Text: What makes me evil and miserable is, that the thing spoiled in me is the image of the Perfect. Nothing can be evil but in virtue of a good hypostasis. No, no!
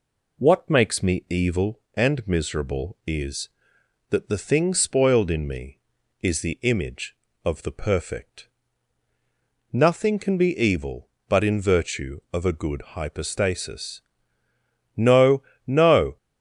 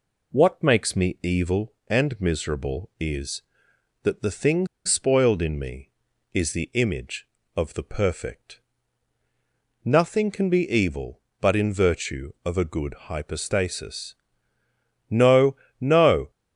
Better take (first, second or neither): first